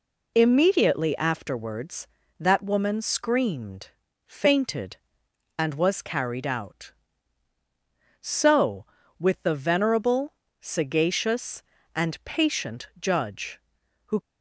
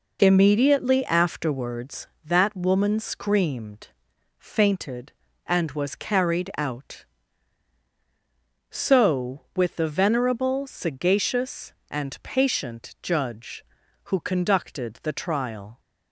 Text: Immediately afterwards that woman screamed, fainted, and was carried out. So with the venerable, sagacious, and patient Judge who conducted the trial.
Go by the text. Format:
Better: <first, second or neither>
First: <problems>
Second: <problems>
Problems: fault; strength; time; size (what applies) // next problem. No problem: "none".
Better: second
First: stops before "conducted the trial"; at 14.1 s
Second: none